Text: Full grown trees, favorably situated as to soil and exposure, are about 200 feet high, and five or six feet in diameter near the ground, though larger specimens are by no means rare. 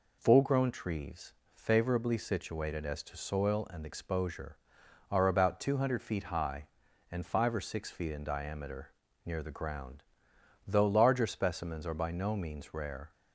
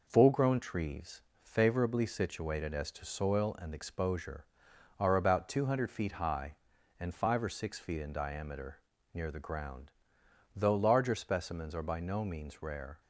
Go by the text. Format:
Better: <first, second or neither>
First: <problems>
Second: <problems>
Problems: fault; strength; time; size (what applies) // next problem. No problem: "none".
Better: first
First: pauses between "diameter" and "near"; slight; at 8.9 s; 0.32 s long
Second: gets quieter; throughout; 3.5 dB // pauses between "diameter" and "near"; slight; at 8.7 s; 0.32 s long